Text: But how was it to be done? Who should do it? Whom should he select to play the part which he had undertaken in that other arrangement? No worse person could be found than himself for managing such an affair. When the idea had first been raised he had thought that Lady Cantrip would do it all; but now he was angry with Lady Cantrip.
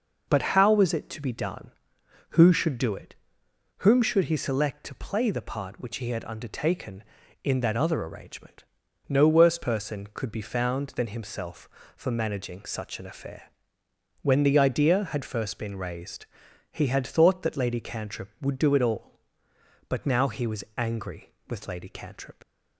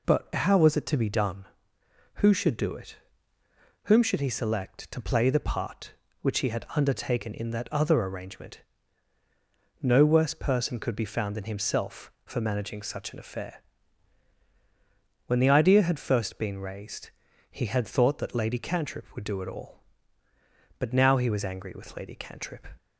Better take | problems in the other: second | pauses between "raised" and "he"; at 16.2 s; 0.44 s long; also in the second // leaves "Cantrip" unfinished; at 22.4 s; 35 ms

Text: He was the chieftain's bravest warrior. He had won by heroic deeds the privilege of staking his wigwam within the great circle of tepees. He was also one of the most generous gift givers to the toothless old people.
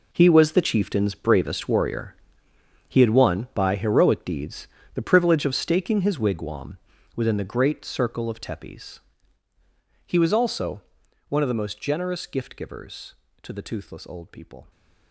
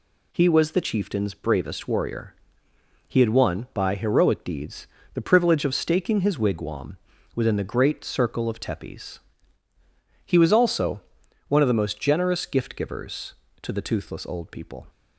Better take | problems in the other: second | gets quieter; strong; throughout; 12.5 dB // pauses between "deeds" and "the"; slight; at 4.6 s; 0.26 s long; slight in the second // pauses between "wigwam" and "within"; at 6.7 s; 0.40 s long; also in the second // pauses between "also" and "one"; noticeable; at 10.8 s; 0.48 s long; noticeable in the second

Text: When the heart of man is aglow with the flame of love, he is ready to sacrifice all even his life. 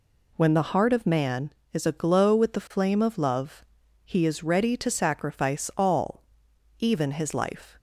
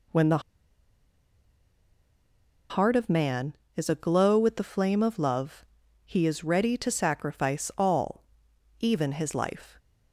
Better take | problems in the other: first | pauses between "the" and "heart"; strong; at 0.4 s; 2.3 s long // pauses between "all" and "even"; noticeable; at 8.2 s; 0.54 s long; noticeable in the first

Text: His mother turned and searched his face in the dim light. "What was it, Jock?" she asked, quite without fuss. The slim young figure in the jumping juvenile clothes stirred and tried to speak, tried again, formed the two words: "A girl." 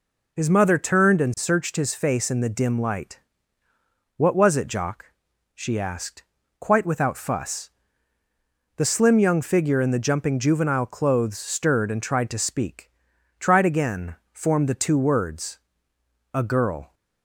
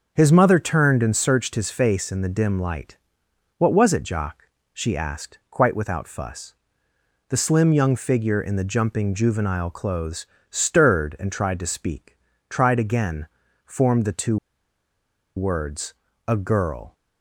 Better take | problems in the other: first | pauses between "clothes" and "stirred"; slight; at 10.2 s; 0.24 s long // pauses between "two" and "words"; at 14.3 s; 1.0 s long

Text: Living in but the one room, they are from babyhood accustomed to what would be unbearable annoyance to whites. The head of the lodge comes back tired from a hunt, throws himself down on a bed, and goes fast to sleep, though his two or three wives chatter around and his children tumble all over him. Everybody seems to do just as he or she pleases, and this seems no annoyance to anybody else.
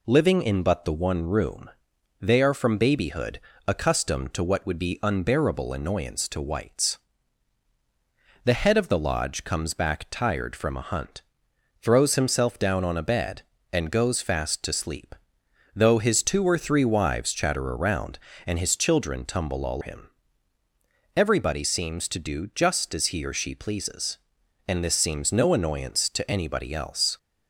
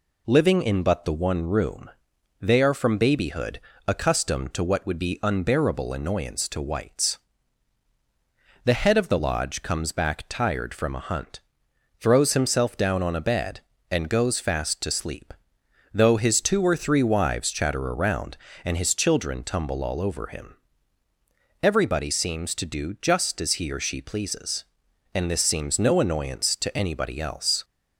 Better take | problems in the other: second | pauses between "babyhood" and "accustomed"; slight; at 3.3 s; 0.28 s long; slight in the second // skips "over"; at 19.8 s

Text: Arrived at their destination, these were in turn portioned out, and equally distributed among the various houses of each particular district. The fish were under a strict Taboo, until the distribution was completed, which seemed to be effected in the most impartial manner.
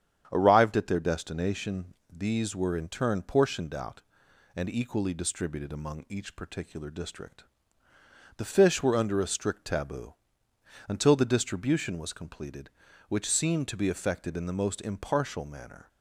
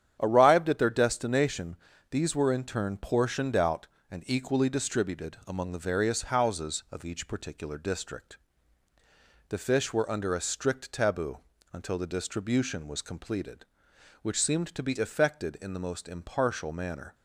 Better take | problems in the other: second | starts louder than the rest; strong; until 1.3 s; 8.5 dB; strong in the second // skips "the various houses of"; at 6.0 s

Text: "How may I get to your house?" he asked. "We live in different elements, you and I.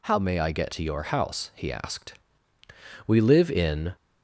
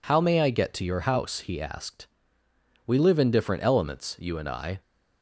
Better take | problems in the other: second | stops before "different elements you and I"; at 3.9 s

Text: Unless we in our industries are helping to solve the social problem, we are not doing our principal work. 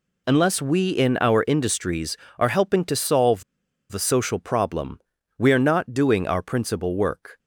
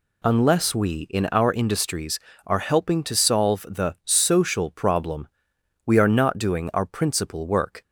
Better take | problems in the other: second | pauses between "solve" and "the"; noticeable; at 3.4 s; 0.49 s long

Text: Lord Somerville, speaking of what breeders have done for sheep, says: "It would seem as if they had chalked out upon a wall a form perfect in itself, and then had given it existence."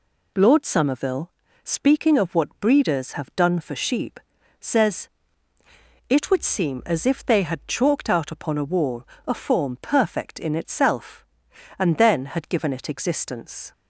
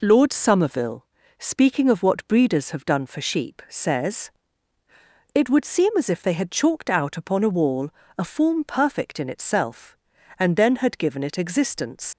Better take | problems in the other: first | pauses between "wall" and "a"; slight; at 7.9 s; 0.26 s long; slight in the first // leaves "existence" unfinished; at 12.1 s; 105 ms

